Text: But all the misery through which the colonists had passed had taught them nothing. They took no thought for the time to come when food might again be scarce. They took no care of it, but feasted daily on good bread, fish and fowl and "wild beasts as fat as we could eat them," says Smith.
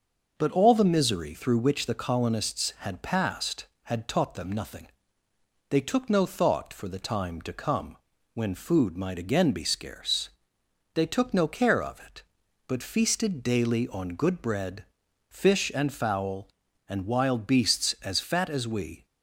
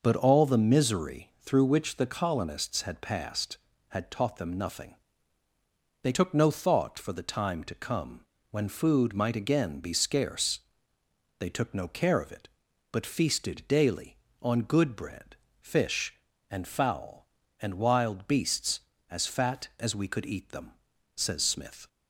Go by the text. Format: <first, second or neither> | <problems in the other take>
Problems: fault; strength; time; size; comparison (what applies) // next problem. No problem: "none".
second | starts louder than the rest; noticeable; until 1.3 s; 6 dB // pauses between "come" and "when"; at 7.9 s; 0.38 s long; slight in the second // stops before "could eat them says Smith"; at 19.0 s